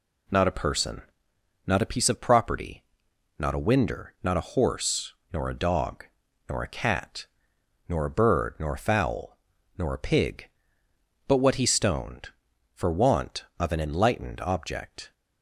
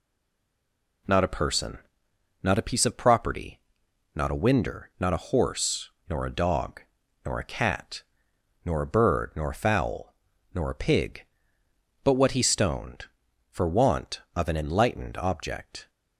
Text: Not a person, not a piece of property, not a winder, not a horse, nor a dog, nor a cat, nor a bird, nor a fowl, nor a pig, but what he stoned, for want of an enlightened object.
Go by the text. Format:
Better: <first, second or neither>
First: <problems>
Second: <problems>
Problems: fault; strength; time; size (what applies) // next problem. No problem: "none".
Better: first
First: none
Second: stays silent before the first word; until 1.0 s; 1.0 s long